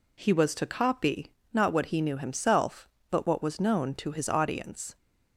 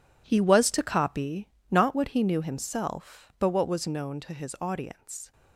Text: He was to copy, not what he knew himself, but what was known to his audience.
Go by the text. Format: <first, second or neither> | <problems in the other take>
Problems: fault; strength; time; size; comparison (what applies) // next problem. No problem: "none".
first | gets quieter; strong; throughout; 13.5 dB